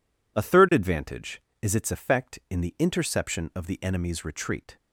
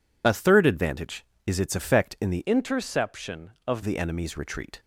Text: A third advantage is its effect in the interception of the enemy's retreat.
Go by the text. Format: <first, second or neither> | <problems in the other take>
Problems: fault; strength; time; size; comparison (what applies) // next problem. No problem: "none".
first | changes voice from "interception" to "of"; from 2.4 to 3.8 s; 1.4 s long